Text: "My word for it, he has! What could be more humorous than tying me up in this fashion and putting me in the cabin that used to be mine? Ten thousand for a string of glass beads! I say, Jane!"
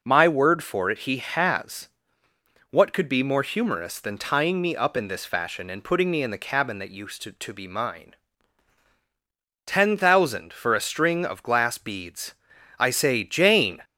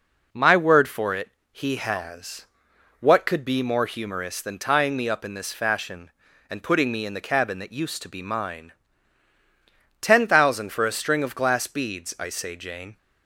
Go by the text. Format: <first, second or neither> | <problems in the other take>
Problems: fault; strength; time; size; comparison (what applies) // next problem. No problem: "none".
second | says "to" twice; at 7.3 s